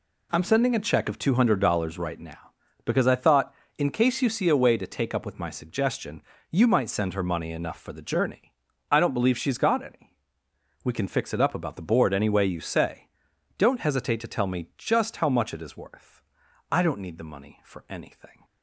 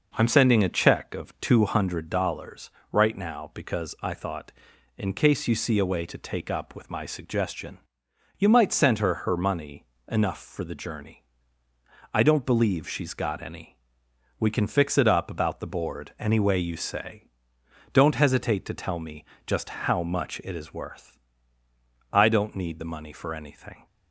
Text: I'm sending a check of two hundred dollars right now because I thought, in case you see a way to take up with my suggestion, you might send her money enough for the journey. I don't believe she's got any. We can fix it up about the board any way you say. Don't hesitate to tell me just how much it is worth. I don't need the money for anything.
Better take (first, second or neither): first